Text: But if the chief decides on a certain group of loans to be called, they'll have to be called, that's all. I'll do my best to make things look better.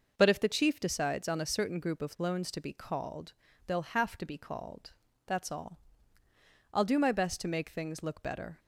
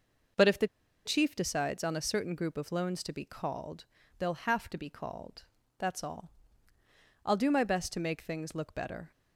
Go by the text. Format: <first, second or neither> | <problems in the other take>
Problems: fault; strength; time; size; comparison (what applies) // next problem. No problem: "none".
first | pauses between "the" and "chief"; at 0.6 s; 0.38 s long